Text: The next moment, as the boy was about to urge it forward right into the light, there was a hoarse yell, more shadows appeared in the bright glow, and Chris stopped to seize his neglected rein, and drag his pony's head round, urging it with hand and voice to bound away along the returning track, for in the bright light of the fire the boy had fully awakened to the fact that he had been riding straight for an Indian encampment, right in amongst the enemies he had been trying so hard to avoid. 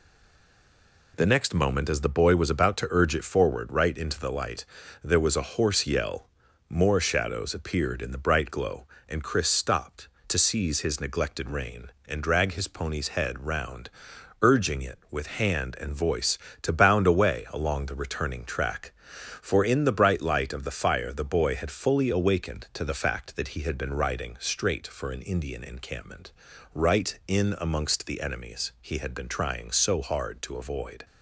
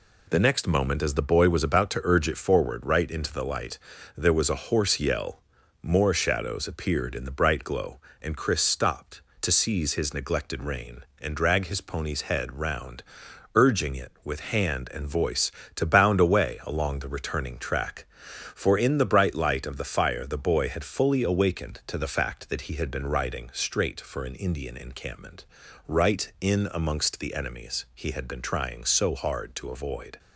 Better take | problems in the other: second | stays silent before the first word; until 1.1 s; 1.1 s long

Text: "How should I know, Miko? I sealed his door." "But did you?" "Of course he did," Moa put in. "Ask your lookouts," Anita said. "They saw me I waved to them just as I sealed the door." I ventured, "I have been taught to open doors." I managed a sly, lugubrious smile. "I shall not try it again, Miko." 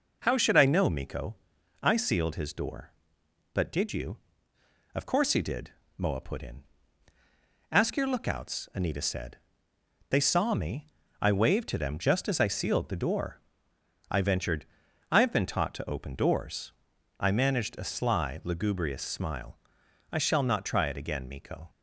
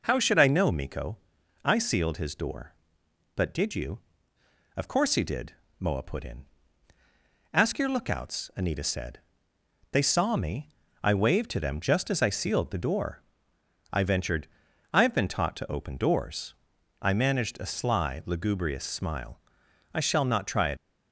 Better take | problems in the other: first | pauses between "me" and "I"; slight; at 10.6 s; 0.34 s long; slight in the first // stops before "again Miko"; at 20.7 s

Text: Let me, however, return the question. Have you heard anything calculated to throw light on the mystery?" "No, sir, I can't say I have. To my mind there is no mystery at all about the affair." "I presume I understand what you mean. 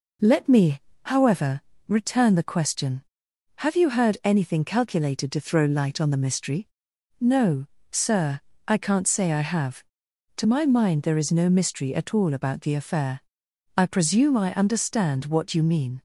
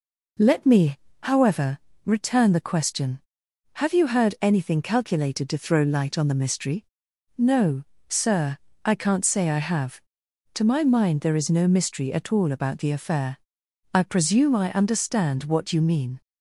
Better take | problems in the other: neither | none

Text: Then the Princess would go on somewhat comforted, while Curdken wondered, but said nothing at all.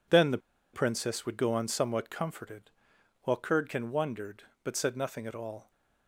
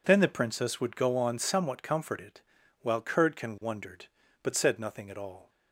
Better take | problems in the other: second | pauses between "the" and "Princess"; slight; at 0.3 s; 0.35 s long

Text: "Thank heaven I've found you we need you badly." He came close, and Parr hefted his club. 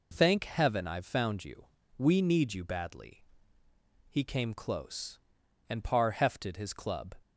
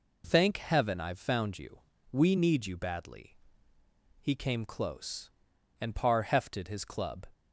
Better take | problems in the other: neither | pauses between "you" and "we"; slight; the same in both

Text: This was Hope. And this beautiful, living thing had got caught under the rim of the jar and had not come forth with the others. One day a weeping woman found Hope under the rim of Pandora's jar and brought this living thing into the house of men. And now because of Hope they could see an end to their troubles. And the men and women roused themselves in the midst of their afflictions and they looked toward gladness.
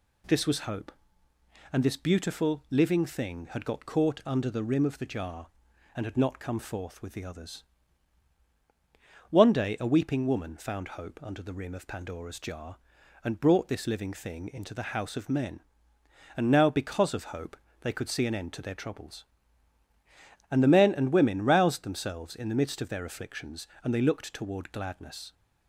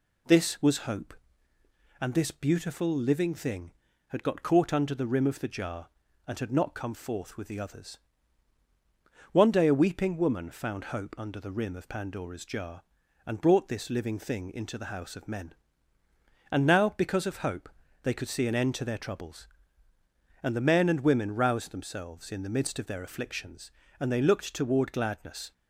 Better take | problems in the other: neither | pauses between "Hope" and "they"; slight; the same in both

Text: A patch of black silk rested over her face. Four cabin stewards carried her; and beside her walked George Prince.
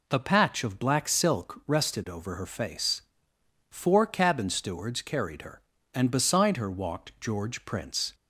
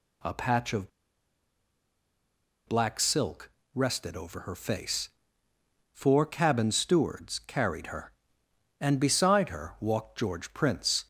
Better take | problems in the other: first | pauses between "of" and "black"; strong; at 0.8 s; 1.7 s long // pauses between "silk" and "rested"; slight; at 3.5 s; 0.24 s long

